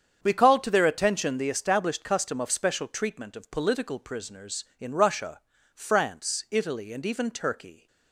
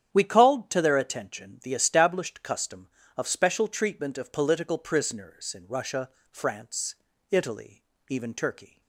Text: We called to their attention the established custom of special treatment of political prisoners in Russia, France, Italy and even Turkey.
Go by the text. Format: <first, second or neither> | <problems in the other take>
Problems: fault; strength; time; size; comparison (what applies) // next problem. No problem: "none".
first | starts louder than the rest; strong; until 1.1 s; 9 dB; strong in the first // skips "and"; at 7.9 s